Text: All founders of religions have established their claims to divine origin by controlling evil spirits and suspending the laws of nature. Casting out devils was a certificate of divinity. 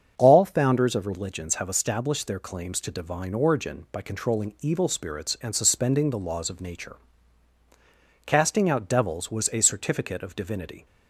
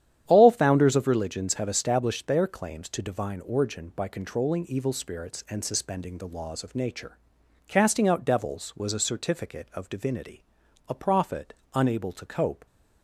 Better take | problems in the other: first | starts louder than the rest; strong; until 1.2 s; 10.5 dB; also in the first // goes on to say "A prophet unable to cope"; strong; from 10.8 s on; 1.7 s long

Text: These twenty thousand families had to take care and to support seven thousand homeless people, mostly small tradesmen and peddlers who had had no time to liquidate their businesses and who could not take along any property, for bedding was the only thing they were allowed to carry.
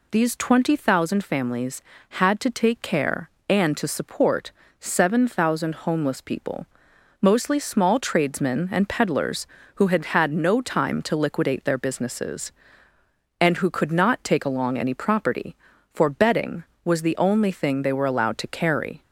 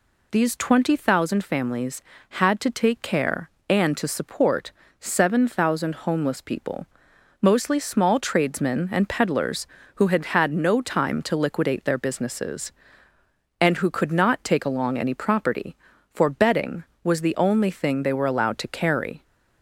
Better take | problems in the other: neither | pauses between "support" and "seven"; slight; the same in both

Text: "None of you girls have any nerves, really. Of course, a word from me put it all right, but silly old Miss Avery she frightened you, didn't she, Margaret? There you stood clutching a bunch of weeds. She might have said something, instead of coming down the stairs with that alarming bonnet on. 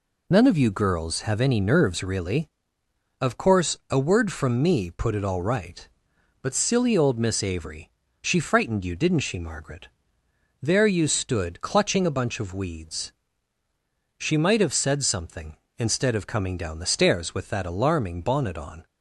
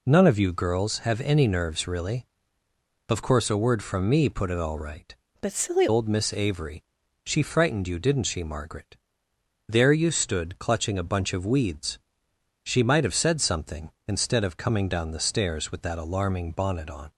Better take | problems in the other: first | changes voice from "but" to "silly"; from 5.4 to 5.8 s; 0.4 s long // pauses between "Avery" and "she"; at 6.8 s; 0.44 s long; slight in the first

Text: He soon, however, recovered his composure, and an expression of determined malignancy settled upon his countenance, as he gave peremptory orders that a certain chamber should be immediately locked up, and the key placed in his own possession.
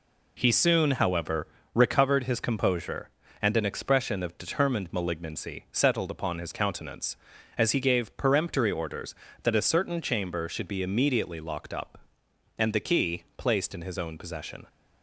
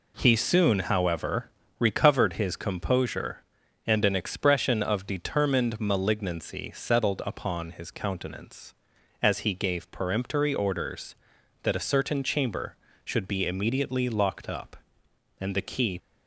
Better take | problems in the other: first | stops before "placed in his own possession"; at 15.9 s

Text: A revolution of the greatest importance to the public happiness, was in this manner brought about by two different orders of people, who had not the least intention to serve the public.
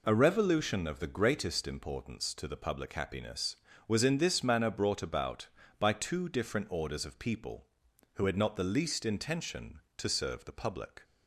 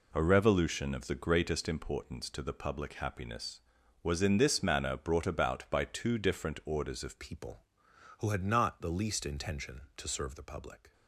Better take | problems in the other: first | changes voice at "people"; from 7.1 s on; 3.8 s long

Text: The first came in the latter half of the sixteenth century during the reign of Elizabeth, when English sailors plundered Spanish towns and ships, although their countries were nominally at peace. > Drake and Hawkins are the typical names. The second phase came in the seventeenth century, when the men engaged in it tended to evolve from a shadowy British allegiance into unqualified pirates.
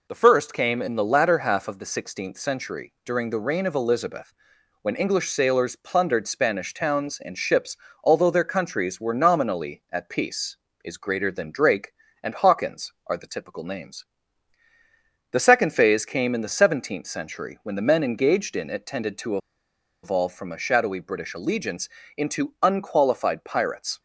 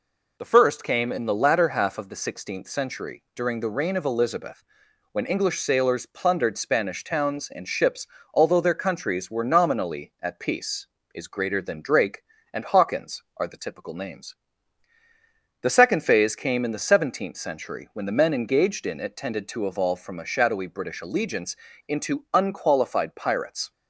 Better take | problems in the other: second | pauses between "to" and "evolve"; noticeable; at 19.3 s; 0.65 s long // pauses between "allegiance" and "into"; slight; at 21.8 s; 0.28 s long; slight in the second

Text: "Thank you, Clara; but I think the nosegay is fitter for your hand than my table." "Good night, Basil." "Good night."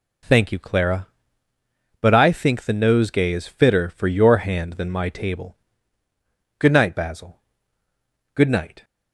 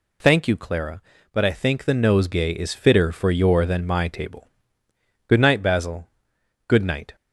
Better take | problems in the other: first | skips "hand"; at 3.6 s

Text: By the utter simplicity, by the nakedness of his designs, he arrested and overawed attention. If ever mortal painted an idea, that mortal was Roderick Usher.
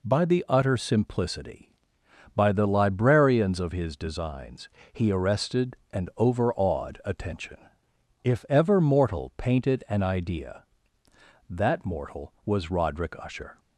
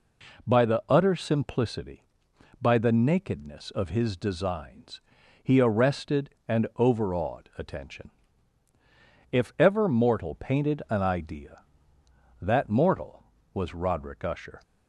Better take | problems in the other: second | says "librarians" for "nakedness"; at 2.6 s

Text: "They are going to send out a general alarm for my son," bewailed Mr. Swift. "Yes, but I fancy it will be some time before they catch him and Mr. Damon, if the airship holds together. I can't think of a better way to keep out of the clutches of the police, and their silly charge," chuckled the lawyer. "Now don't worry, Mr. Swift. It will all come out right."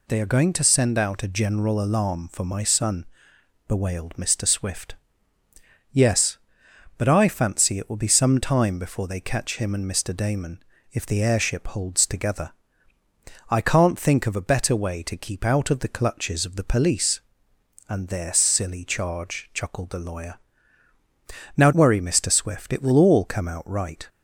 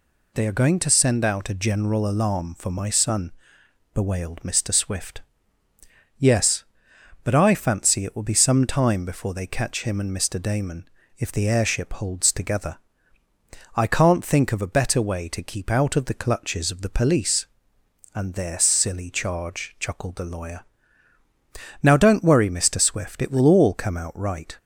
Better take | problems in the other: second | skips "don't"; at 21.7 s

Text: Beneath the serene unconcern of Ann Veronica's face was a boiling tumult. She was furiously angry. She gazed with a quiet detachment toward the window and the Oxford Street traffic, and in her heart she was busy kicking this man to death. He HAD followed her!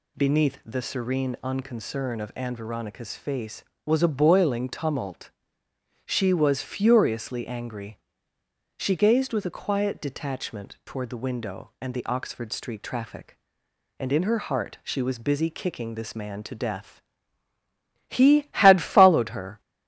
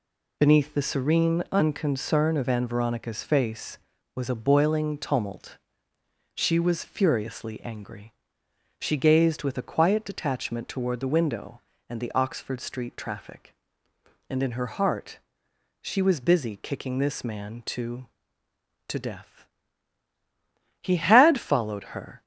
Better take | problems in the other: first | pauses between "heart" and "she"; noticeable; at 15.1 s; 0.64 s long // says "to" twice; at 18.8 s

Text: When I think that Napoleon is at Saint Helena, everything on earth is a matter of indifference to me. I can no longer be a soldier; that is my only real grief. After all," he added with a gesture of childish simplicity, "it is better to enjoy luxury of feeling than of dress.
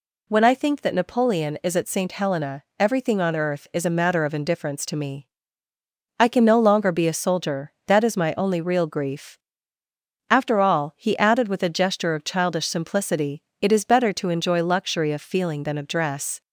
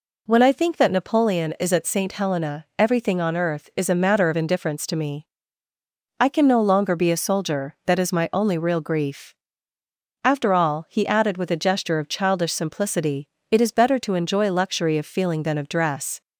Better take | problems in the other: neither | none

